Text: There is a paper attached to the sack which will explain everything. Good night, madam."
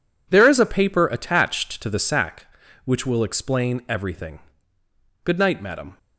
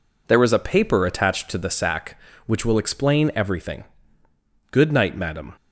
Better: second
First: gets quieter; strong; throughout; 12 dB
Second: none

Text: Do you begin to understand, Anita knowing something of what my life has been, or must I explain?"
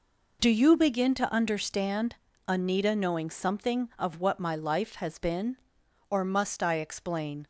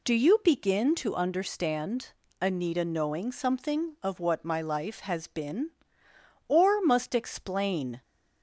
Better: first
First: none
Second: skips "I"; at 7.1 s

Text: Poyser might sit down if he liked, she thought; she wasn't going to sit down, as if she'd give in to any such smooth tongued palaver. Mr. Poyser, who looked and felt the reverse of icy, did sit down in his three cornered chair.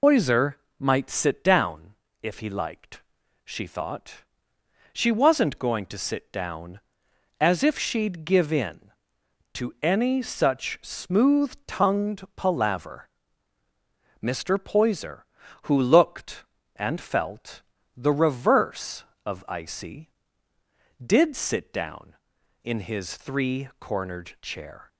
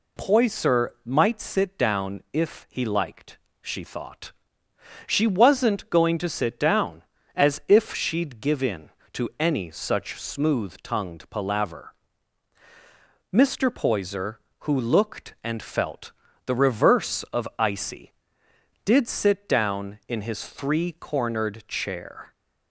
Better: second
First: loses the start of "Poyser"; at 0.0 s; 90 ms // pauses between "Poyser" and "might"; slight; at 0.5 s; 0.26 s long // pauses between "down" and "if"; slight; at 1.9 s; 0.28 s long // pauses between "felt" and "the"; slight; at 17.5 s; 0.34 s long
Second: pauses between "Poyser" and "might"; slight; at 0.8 s; 0.16 s long // pauses between "felt" and "the"; slight; at 16.1 s; 0.34 s long

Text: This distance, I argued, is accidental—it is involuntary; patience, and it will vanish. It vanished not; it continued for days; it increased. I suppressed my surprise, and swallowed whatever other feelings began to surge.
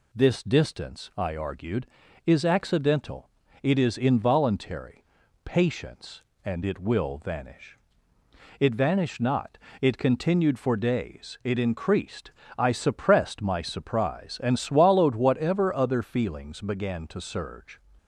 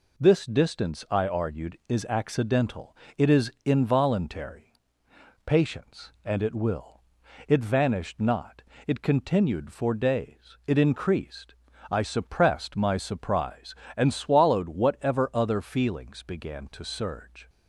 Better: first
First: none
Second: skips "vanish"; at 7.2 s

